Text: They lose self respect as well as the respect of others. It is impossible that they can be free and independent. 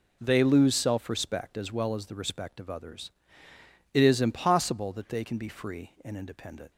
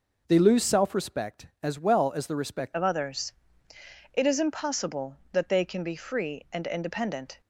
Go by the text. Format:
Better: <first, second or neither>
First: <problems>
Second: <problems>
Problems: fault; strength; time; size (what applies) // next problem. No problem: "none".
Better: first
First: none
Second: changes voice at "of"; from 2.7 s on; 4.7 s long